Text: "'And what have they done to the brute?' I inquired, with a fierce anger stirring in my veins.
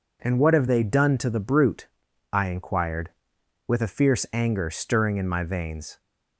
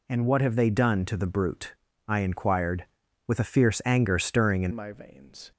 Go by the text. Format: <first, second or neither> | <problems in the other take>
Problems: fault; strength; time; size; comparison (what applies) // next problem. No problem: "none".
first | changes voice at "my"; from 4.7 s on; 0.8 s long